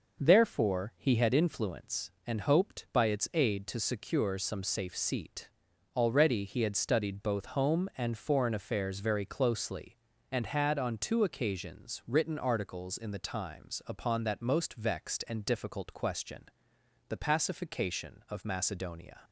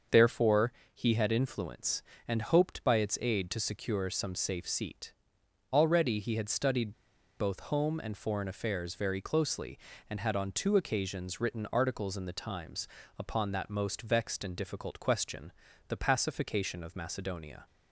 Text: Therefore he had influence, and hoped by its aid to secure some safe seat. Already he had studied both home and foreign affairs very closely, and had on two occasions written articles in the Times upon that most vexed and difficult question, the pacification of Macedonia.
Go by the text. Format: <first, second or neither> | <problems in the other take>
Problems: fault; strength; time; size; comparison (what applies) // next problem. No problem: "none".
first | starts louder than the rest; until 1.3 s; 6.5 dB // pauses between "Therefore" and "he"; slight; at 0.7 s; 0.20 s long // pauses between "studied" and "both"; noticeable; at 6.9 s; 0.48 s long // pauses between "Times" and "upon"; slight; at 12.8 s; 0.30 s long